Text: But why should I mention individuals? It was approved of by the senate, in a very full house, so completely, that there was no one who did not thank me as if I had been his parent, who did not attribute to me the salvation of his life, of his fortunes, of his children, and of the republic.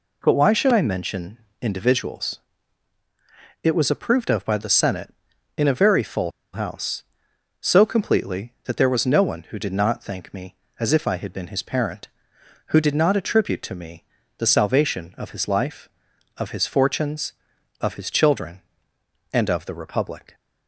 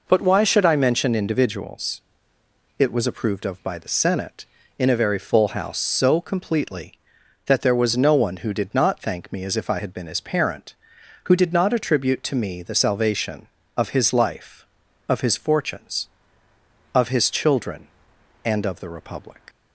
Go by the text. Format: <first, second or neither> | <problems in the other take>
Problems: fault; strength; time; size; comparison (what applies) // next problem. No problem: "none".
second | pauses between "mention" and "individuals"; slight; at 1.3 s; 0.24 s long // pauses between "full" and "house"; slight; at 6.3 s; 0.22 s long // pauses between "me" and "the"; slight; at 14.0 s; 0.32 s long